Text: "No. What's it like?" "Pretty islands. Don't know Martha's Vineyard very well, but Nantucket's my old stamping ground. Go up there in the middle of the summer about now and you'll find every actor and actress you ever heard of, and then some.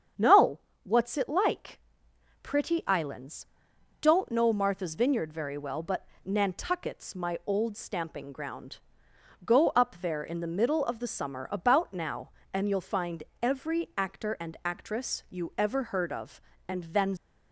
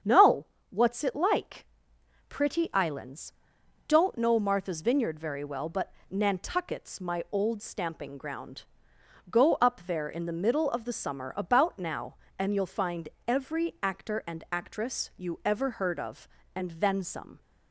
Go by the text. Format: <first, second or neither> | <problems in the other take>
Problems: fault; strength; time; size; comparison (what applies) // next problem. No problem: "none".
second | starts louder than the rest; strong; until 1.4 s; 8 dB; strong in the second // pauses between "but" and "Nantucket's"; slight; at 6.0 s; 0.16 s long; slight in the second // pauses between "find" and "every"; slight; at 13.2 s; 0.20 s long; slight in the second // stops before "some"; at 17.1 s